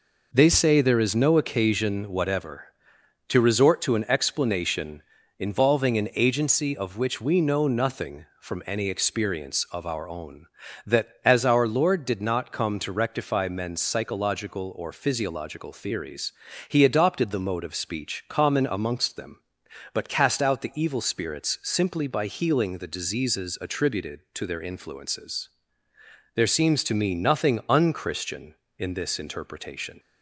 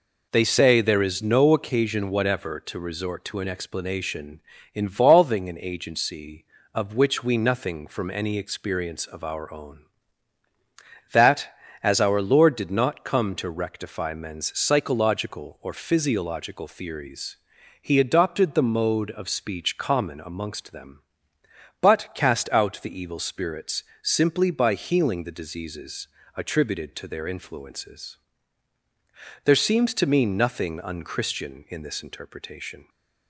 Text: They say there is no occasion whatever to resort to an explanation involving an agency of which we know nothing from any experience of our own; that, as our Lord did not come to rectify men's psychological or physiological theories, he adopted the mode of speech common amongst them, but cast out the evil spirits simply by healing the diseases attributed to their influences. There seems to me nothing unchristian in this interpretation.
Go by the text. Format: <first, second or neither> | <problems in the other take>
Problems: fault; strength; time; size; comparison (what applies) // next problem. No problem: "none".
first | pauses between "explanation" and "involving"; slight; at 4.4 s; 0.34 s long; slight in the first // skips "know"; at 7.3 s // pauses between "spirits" and "simply"; slight; at 23.8 s; 0.20 s long // pauses between "diseases" and "attributed"; slight; at 26.0 s; 0.30 s long